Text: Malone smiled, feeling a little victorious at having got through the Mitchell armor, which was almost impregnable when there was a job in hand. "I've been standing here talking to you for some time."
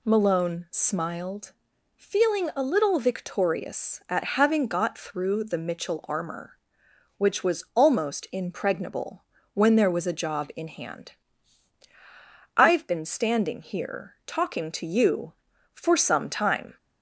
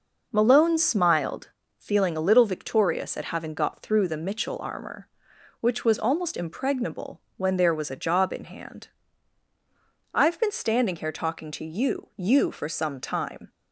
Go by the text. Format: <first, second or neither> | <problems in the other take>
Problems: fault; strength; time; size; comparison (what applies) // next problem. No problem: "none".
first | pauses between "impregnable" and "when"; slight; at 7.1 s; 0.18 s long; slight in the first // says "you" twice; at 12.1 s